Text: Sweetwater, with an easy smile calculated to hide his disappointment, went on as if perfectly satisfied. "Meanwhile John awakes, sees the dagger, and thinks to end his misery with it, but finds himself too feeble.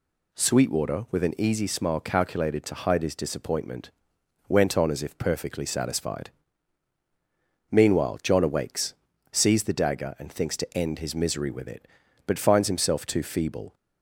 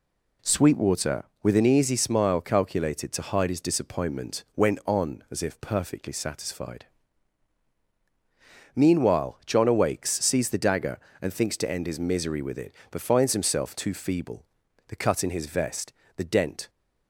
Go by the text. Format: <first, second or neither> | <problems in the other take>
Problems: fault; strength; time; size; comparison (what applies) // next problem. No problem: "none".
first | goes on to say "The cut in his vest the dent"; strong; from 14.8 s on; 1.8 s long